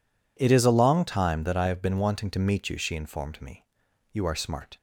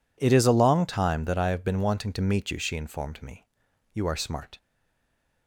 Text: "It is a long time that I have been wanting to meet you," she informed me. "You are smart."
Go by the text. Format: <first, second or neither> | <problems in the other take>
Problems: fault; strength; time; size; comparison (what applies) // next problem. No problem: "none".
first | stays silent after the last word; slight; from 4.5 s on; 0.9 s long